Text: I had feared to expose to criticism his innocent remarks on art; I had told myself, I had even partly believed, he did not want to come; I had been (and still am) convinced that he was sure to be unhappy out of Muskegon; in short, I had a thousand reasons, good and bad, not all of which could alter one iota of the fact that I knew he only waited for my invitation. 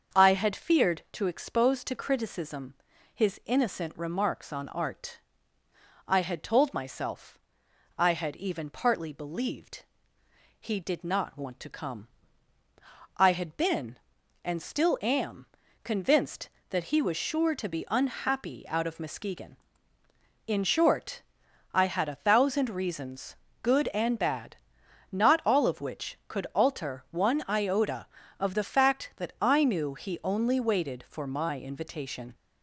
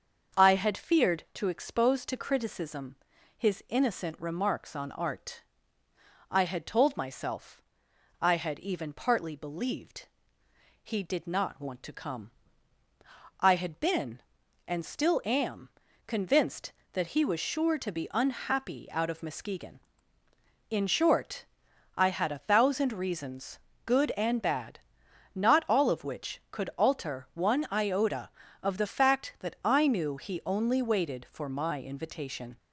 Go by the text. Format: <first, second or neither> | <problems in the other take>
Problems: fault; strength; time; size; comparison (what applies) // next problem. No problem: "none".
neither | starts louder than the rest; the same in both // pauses between "criticism" and "his"; the same in both